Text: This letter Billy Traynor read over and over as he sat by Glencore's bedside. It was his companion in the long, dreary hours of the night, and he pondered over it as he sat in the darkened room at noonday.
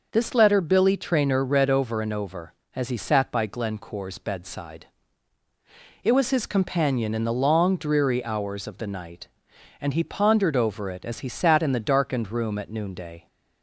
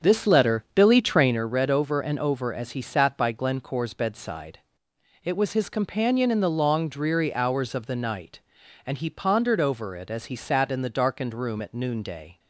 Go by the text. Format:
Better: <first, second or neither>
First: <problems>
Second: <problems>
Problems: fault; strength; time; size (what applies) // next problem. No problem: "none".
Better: first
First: none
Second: starts louder than the rest; strong; until 1.4 s; 7 dB